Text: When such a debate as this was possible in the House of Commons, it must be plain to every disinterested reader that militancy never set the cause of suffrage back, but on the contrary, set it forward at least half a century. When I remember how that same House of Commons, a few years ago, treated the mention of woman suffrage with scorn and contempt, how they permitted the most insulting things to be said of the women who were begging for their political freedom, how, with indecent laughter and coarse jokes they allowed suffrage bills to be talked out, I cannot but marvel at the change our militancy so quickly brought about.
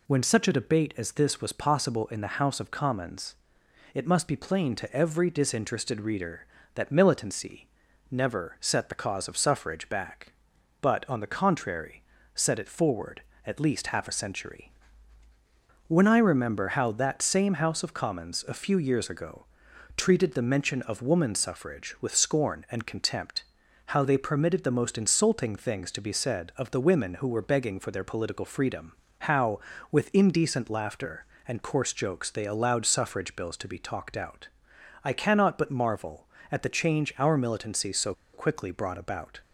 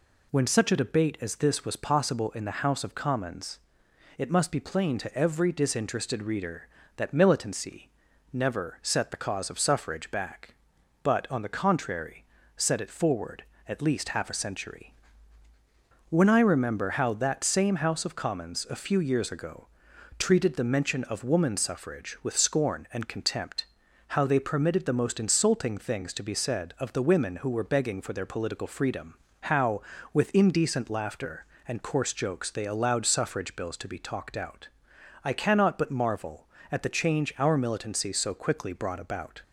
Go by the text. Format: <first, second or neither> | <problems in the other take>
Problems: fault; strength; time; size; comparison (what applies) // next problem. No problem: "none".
second | pauses between "militancy" and "never"; at 7.6 s; 0.42 s long; also in the second // pauses between "so" and "quickly"; slight; at 38.1 s; 0.21 s long